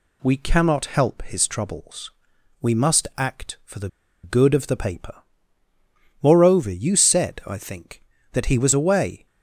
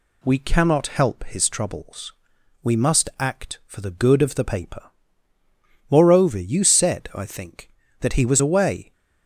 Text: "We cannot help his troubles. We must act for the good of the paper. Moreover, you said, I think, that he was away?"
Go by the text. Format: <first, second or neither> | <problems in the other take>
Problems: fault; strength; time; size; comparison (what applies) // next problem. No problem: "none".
second | pauses between "the" and "good"; slight; at 3.8 s; 0.35 s long